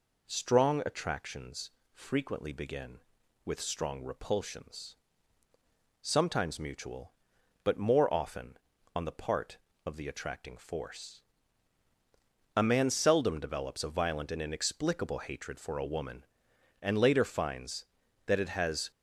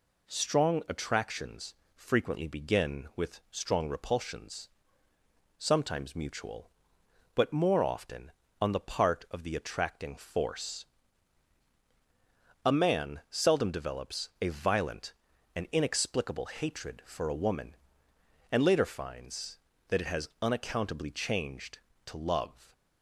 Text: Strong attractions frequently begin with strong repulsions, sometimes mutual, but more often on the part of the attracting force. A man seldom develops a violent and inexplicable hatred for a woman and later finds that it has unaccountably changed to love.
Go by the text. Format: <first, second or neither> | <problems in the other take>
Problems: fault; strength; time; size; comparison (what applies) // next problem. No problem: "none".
second | pauses between "attractions" and "frequently"; slight; at 1.7 s; 0.22 s long; slight in the second // stops before "unaccountably changed to love"; at 18.9 s